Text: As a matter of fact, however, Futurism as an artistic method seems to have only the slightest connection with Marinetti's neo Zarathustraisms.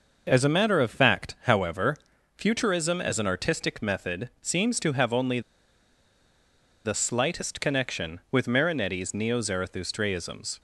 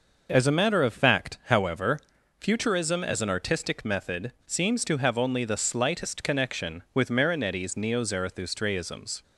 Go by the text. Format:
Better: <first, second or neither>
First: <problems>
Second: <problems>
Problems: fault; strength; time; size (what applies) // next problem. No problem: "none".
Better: second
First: pauses between "only" and "the"; strong; at 5.3 s; 1.4 s long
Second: none